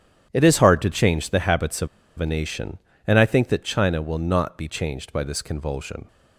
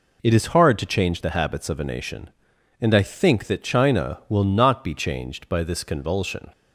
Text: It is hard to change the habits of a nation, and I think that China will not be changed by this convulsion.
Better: second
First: starts louder than the rest; strong; until 1.3 s; 10 dB // pauses between "of" and "a"; slight; at 1.8 s; 0.31 s long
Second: none

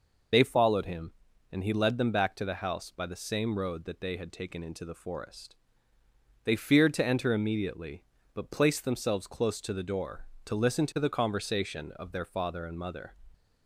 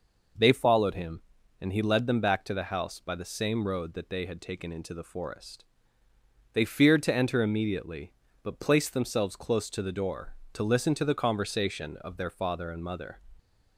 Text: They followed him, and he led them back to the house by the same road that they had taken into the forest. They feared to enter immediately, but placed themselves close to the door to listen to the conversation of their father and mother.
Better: second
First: loses the start of "They"; at 0.3 s; 65 ms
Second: none

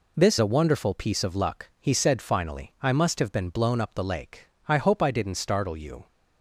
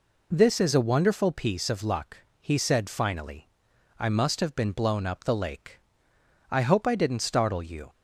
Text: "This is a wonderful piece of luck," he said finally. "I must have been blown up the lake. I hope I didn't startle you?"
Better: second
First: skips "is"; at 0.3 s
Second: none

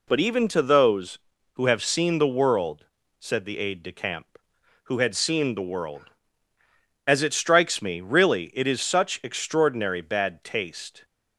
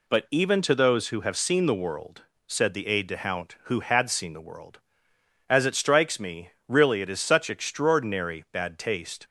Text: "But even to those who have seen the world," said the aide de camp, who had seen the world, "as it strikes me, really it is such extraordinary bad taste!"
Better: first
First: none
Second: says "hount" for "camp"; at 3.1 s

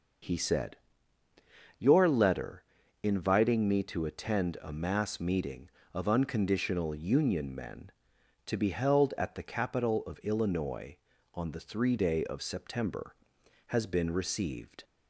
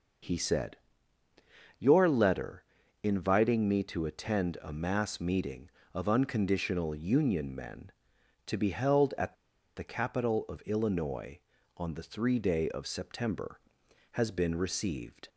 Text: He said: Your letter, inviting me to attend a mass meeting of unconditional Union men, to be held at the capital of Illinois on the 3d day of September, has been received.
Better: first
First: none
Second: pauses between "at" and "the"; at 9.3 s; 0.40 s long

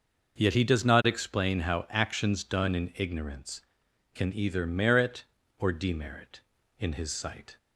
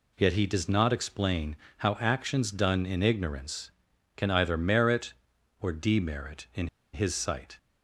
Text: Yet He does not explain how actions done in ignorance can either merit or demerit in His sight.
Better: first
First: none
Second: pauses between "explain" and "how"; slight; at 1.5 s; 0.22 s long // pauses between "in" and "His"; slight; at 6.6 s; 0.26 s long

